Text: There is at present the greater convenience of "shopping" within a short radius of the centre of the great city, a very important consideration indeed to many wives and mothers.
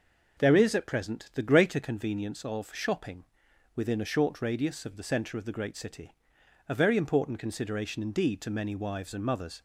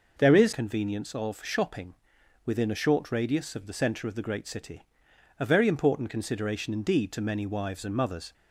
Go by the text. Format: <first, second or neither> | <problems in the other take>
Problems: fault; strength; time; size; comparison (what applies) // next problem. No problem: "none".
first | skips "at present the greater"; at 0.5 s // pauses between "shopping" and "within"; noticeable; at 1.9 s; 0.50 s long; noticeable in the first